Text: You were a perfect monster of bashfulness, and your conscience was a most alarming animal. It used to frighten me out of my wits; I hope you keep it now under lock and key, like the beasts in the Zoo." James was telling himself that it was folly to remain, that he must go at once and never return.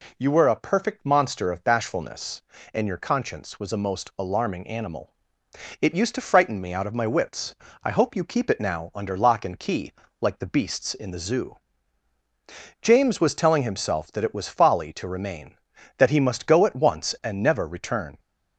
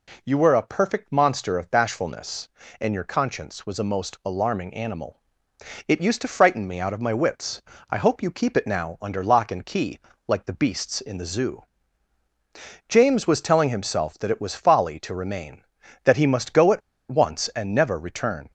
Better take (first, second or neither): first